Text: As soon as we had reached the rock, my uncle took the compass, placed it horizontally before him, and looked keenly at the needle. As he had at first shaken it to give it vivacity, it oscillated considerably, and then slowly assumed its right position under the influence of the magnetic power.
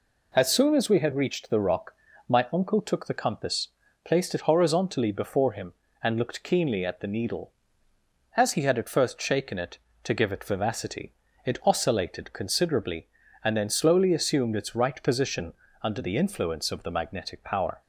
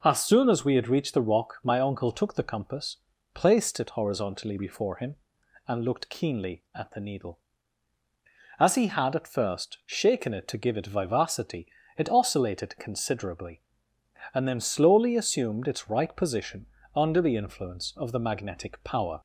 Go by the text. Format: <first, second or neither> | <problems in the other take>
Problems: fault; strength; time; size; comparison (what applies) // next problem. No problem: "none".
neither | pauses between "position" and "under"; slight; the same in both